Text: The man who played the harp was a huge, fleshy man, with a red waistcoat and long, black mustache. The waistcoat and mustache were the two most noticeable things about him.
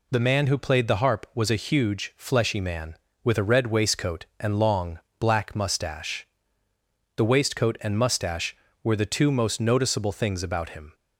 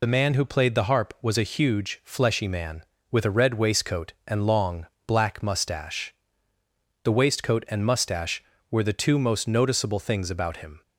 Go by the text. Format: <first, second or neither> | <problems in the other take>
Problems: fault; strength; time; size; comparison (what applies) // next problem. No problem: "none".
first | loses the start of "The"; at 0.0 s; 45 ms